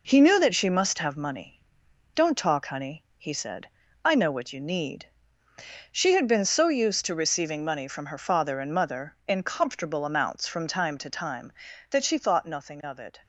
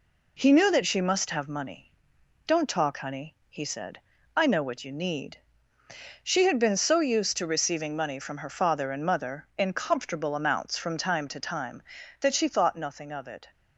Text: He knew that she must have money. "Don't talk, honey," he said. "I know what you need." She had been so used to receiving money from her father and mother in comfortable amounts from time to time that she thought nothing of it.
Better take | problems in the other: second | gets quieter; noticeable; throughout; 6 dB

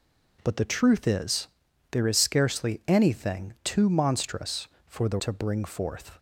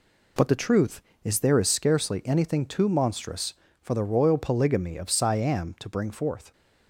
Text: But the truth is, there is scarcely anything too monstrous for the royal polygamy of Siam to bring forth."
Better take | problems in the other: second | skips "royal polygamy of Siam"; at 5.1 s

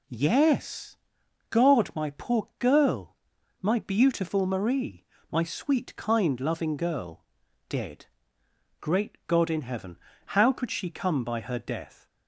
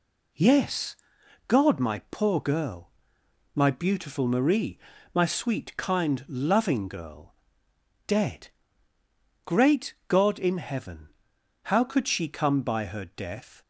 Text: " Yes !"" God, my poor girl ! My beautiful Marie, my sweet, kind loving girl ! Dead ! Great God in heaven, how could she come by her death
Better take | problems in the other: neither | none

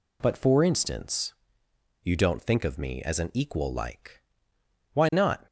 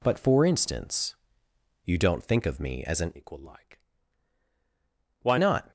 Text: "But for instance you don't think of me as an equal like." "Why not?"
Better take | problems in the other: first | pauses between "instance" and "you"; noticeable; at 1.1 s; 0.70 s long; noticeable in the first // changes voice from "equal" to "Why"; from 3.1 to 5.3 s; 2.2 s long

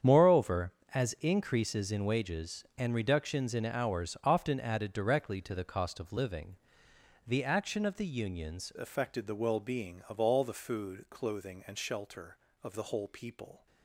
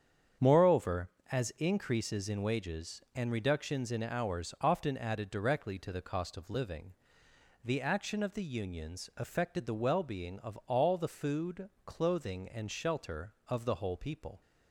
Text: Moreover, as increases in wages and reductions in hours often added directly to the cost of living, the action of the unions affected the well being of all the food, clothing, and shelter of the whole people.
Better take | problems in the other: second | starts louder than the rest; strong; until 1.3 s; 8 dB; strong in the second // changes voice at "affected"; from 8.7 s on; 4.9 s long

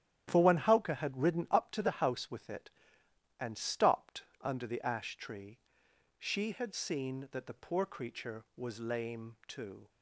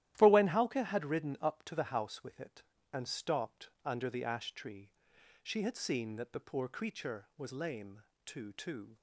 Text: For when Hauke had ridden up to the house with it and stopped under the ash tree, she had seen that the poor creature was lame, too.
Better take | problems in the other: first | starts louder than the rest; strong; until 1.1 s; 13 dB; strong in the first // pauses between "stopped" and "under"; slight; at 3.6 s; 0.16 s long; slight in the first // says "too" twice; at 8.5 s

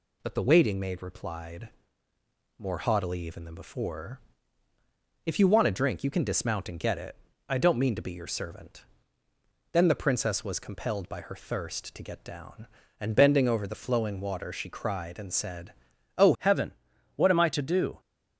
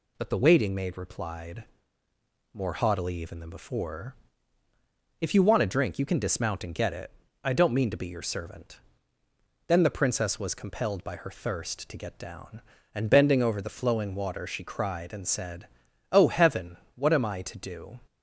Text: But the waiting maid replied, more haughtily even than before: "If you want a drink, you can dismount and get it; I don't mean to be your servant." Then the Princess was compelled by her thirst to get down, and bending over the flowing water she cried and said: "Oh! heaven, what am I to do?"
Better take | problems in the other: second | changes voice at "heaven"; from 16.3 s on; 1.6 s long

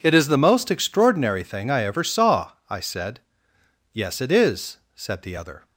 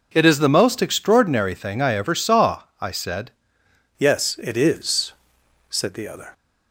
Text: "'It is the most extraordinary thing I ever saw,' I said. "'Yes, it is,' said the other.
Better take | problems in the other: first | changes voice at "Yes"; from 3.9 s on; 2.4 s long

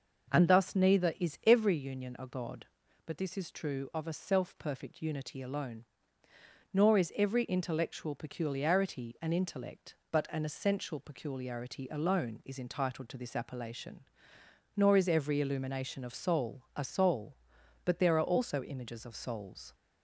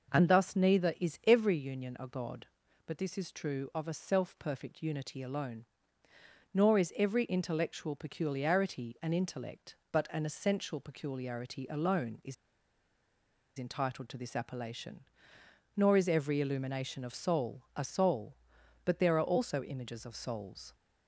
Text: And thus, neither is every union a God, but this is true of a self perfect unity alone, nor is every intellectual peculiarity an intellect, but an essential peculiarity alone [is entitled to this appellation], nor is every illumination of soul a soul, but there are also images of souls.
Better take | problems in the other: first | pauses between "is" and "entitled"; at 12.3 s; 1.2 s long

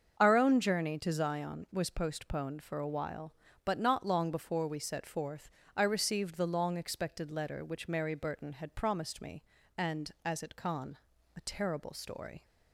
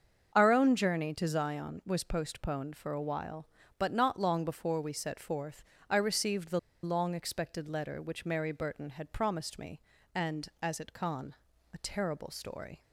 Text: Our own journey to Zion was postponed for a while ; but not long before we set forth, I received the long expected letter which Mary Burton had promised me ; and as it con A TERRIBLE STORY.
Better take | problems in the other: first | starts louder than the rest; until 1.3 s; 7 dB; also in the first // pauses between "the" and "long"; slight; at 6.5 s; 0.24 s long // pauses between "con" and "A"; slight; at 11.3 s; 0.36 s long; slight in the first

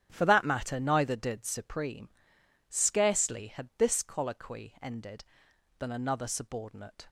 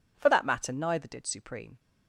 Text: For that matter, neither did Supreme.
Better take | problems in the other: second | starts louder than the rest; strong; until 1.1 s; 9 dB // goes on to say "Scarcely had this colloquy ended than another subordinate"; strong; from 2.6 s on; 4.3 s long

